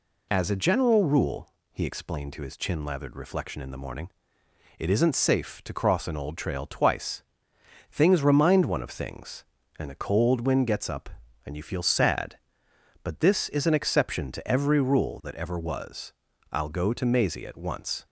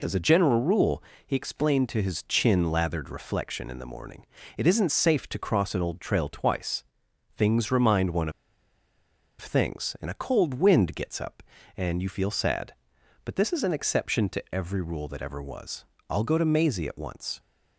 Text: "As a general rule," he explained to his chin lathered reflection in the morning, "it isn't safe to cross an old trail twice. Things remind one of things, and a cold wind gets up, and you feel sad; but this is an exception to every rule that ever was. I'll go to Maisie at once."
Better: first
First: none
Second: pauses between "of" and "things"; at 8.3 s; 1.0 s long

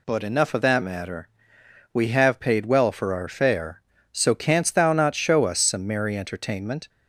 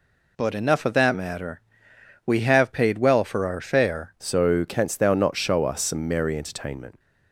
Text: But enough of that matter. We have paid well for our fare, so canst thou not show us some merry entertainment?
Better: first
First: none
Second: changes voice at "so"; from 4.1 s on; 2.8 s long

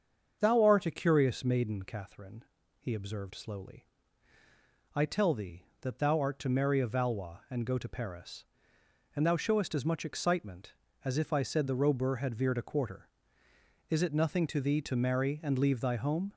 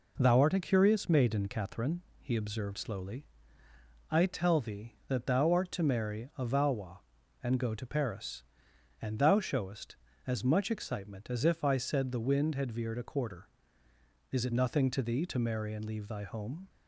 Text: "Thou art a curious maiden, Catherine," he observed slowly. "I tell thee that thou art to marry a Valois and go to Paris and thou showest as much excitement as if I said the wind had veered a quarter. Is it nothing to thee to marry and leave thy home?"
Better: second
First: starts louder than the rest; until 1.4 s; 7 dB // says "robur" for "wind"; at 11.7 s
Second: none

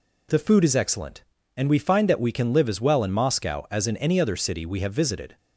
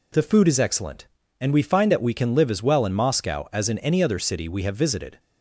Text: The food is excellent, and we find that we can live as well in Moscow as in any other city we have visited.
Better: neither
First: none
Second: none

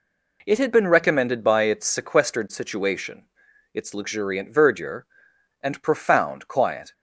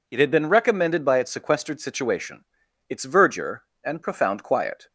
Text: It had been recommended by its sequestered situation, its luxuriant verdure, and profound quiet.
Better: first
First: none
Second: skips "luxuriant"; at 3.0 s

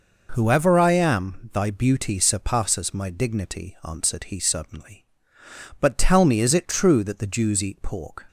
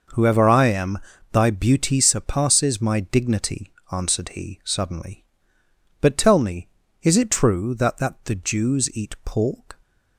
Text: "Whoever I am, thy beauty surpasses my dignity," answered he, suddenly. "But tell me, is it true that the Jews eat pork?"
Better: first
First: none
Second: says "that" twice; at 7.9 s

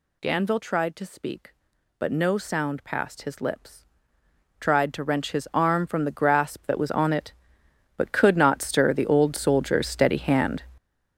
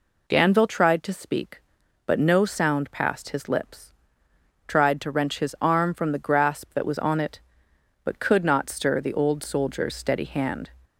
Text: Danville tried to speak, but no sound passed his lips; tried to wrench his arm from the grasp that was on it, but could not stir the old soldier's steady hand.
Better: second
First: gets louder; strong; throughout; 10.5 dB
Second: none

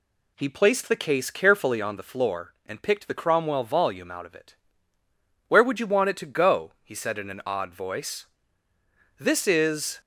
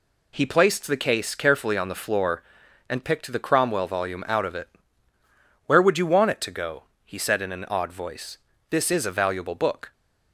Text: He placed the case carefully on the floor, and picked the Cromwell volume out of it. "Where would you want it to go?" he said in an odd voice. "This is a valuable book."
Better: second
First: stops before "a valuable book"; at 10.0 s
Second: none

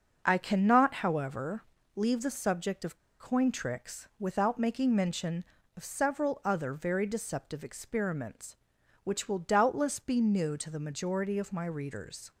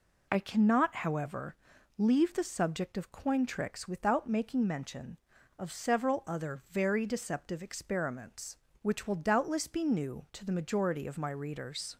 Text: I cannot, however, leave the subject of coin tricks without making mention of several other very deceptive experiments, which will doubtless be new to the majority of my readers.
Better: second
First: starts louder than the rest; until 1.2 s; 6 dB // pauses between "of" and "coin"; slight; at 2.9 s; 0.23 s long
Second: none

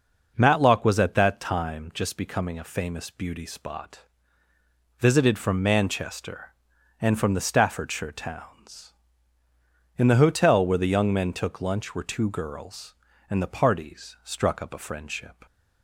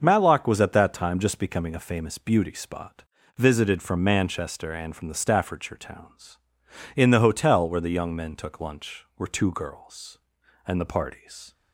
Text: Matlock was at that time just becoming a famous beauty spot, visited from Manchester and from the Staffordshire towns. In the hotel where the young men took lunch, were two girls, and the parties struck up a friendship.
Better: first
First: none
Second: starts louder than the rest; until 1.0 s; 6 dB // stops before "struck up a friendship"; at 11.5 s

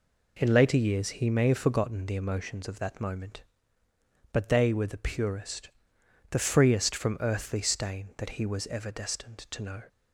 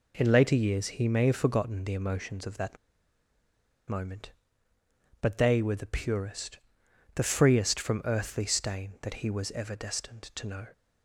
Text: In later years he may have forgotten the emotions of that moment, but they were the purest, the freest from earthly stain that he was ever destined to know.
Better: first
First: none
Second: pauses between "that" and "moment"; at 2.7 s; 1.1 s long

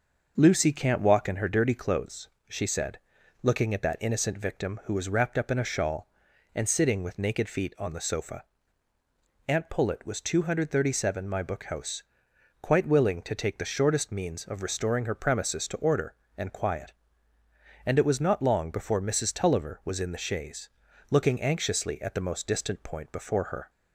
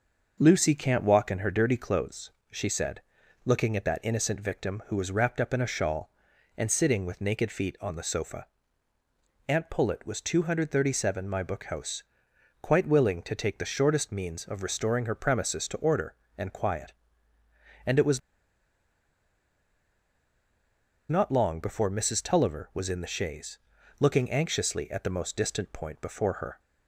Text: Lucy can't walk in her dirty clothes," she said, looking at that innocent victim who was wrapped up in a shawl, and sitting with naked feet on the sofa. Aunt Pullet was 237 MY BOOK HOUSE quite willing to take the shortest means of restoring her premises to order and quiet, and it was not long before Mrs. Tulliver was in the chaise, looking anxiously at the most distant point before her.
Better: first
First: starts louder than the rest; noticeable; until 1.3 s; 6 dB // pauses between "HOUSE" and "quite"; noticeable; at 12.0 s; 0.58 s long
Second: starts louder than the rest; noticeable; until 1.4 s; 6 dB // pauses between "HOUSE" and "quite"; noticeable; at 12.0 s; 0.58 s long // pauses between "was" and "not"; strong; at 18.1 s; 2.8 s long

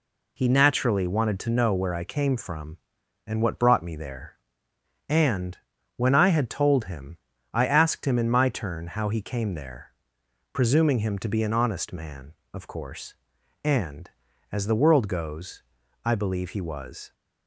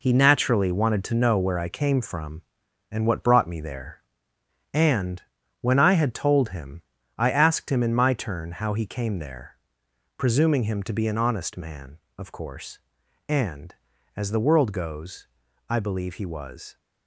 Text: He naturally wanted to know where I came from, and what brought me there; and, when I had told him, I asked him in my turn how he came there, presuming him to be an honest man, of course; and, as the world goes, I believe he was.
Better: first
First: none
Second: gets quieter; strong; throughout; 8.5 dB

